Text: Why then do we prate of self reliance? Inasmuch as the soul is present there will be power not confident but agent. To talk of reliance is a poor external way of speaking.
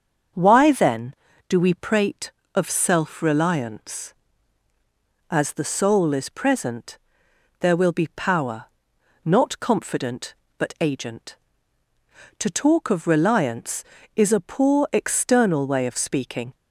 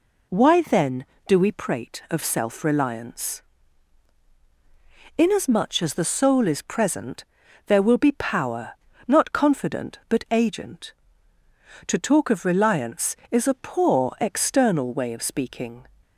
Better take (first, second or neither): second